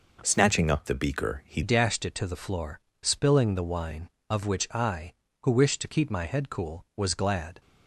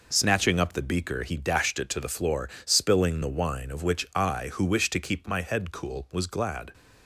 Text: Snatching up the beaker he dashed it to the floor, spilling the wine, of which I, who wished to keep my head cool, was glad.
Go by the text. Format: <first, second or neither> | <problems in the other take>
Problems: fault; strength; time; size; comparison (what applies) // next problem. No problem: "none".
second | changes voice at "dashed"; from 1.6 s on; 6.0 s long